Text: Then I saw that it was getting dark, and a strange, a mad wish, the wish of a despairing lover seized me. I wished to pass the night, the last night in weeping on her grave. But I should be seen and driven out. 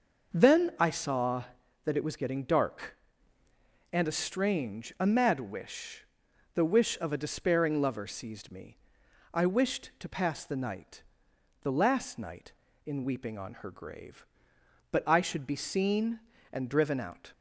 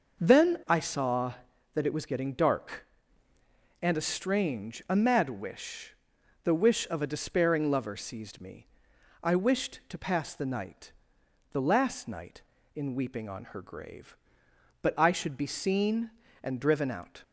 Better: neither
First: none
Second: none

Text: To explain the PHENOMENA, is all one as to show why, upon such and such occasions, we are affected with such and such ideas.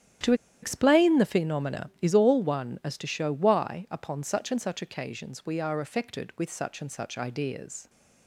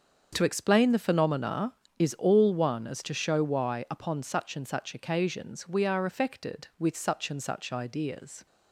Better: second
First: starts louder than the rest; strong; until 1.5 s; 10.5 dB // pauses between "To" and "explain"; slight; at 0.3 s; 0.28 s long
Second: starts louder than the rest; until 1.3 s; 7 dB

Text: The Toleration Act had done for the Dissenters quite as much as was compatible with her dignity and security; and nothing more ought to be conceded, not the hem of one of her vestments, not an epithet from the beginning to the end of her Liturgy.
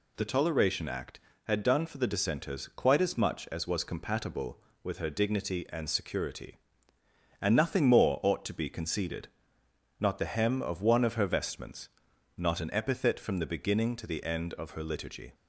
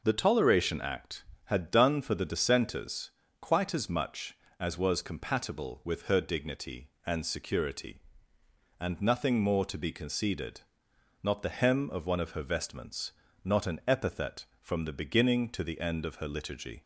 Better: first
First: none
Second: pauses between "Dissenters" and "quite"; slight; at 3.1 s; 0.28 s long // skips "ought"; at 9.6 s

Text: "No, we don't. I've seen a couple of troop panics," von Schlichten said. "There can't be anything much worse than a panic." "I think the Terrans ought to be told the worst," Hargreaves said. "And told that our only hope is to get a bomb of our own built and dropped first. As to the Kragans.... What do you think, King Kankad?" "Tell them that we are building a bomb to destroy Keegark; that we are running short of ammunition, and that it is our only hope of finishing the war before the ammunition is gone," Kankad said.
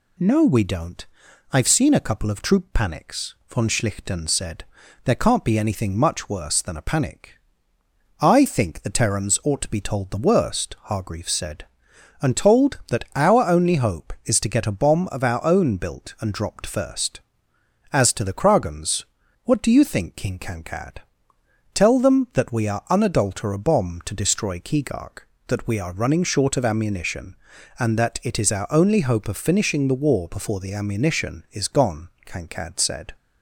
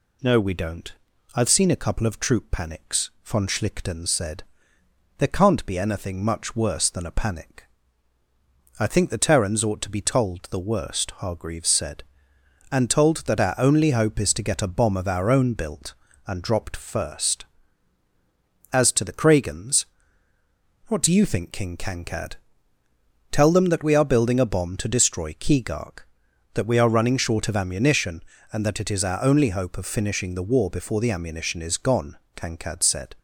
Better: second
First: says "unadulter" for "building"; at 22.9 s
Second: none

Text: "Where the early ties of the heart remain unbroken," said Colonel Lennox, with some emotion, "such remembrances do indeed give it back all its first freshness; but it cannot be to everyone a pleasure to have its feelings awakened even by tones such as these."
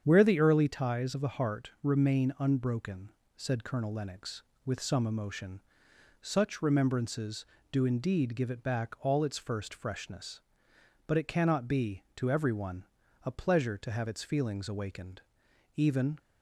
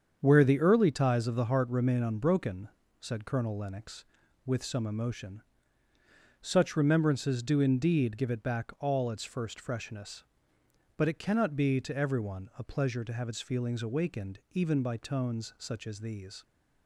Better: second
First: starts louder than the rest; strong; until 1.0 s; 8 dB // pauses between "everyone" and "a"; at 12.8 s; 0.40 s long // pauses between "awakened" and "even"; noticeable; at 15.2 s; 0.54 s long // stops before "by tones such as these"; at 16.1 s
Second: starts louder than the rest; strong; until 1.2 s; 7.5 dB

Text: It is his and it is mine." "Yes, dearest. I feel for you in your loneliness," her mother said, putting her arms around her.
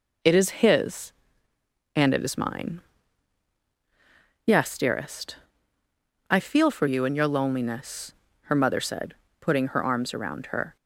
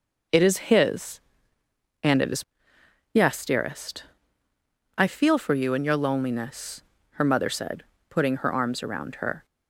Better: first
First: none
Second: skips "mine"; at 2.7 s

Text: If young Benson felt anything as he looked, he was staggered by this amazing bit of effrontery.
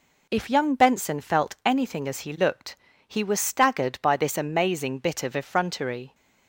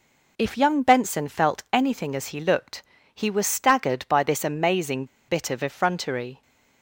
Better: first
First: none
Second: pauses between "amazing" and "bit"; slight; at 5.0 s; 0.23 s long

